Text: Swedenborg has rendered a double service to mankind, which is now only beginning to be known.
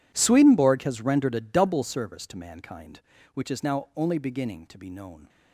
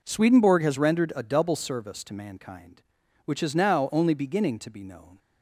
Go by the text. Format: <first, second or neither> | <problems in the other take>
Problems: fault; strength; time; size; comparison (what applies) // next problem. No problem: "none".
second | gets quieter; strong; throughout; 19.5 dB